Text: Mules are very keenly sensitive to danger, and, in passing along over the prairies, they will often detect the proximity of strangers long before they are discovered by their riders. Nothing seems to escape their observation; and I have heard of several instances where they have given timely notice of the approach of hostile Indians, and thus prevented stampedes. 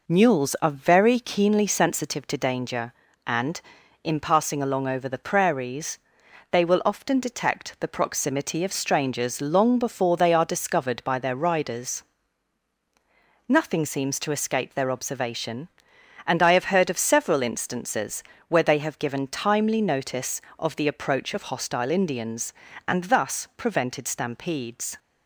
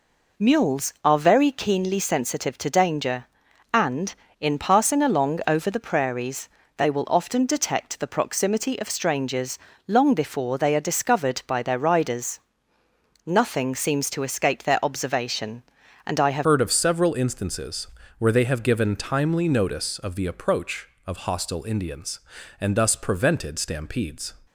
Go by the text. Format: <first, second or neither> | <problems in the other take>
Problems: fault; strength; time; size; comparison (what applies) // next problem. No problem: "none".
first | pauses between "strangers" and "long"; slight; at 9.5 s; 0.30 s long // changes voice at "heard"; from 16.4 s on; 7.9 s long // pauses between "instances" and "where"; slight; at 17.8 s; 0.30 s long; slight in the first